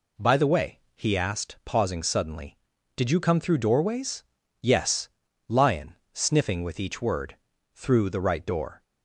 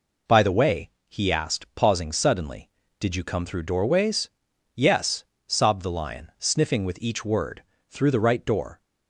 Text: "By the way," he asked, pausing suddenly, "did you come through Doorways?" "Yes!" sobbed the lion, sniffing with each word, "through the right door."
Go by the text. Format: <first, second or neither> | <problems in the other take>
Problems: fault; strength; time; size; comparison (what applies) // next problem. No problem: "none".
second | skips "sobbed the"; at 5.2 s